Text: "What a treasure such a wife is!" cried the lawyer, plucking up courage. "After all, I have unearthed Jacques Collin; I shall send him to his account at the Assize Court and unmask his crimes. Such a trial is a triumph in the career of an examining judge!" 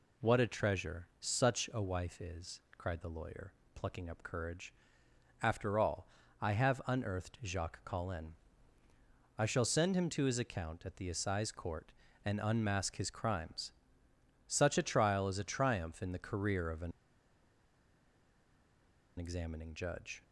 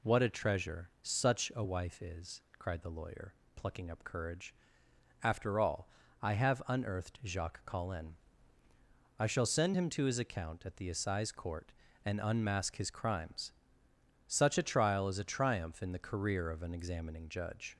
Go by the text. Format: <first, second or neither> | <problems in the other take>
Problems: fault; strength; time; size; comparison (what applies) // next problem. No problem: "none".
second | pauses between "an" and "examining"; strong; at 16.9 s; 2.2 s long